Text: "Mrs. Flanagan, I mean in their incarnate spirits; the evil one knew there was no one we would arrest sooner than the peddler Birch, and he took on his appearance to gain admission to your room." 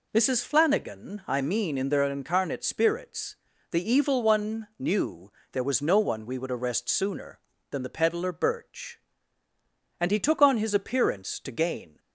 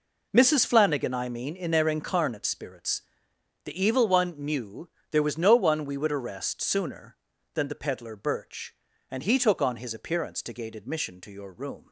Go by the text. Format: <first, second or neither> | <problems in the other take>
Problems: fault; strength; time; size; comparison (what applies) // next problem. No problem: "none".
second | pauses between "knew" and "there"; slight; at 5.3 s; 0.20 s long; slight in the second // stops before "admission to your room"; at 11.9 s